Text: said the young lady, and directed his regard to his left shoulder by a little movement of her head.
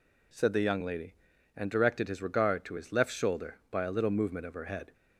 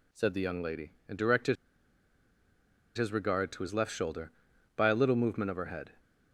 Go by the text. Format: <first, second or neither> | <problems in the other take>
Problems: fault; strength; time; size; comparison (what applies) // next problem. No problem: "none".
first | pauses between "directed" and "his"; strong; at 1.5 s; 1.4 s long